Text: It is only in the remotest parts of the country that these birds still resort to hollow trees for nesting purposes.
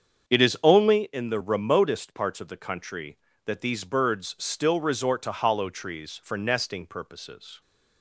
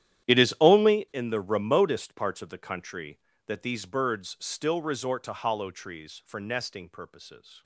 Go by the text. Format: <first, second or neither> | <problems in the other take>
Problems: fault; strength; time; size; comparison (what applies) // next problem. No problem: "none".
first | gets quieter; strong; throughout; 16.5 dB // starts louder than the rest; strong; until 1.3 s; 11 dB; strong in the first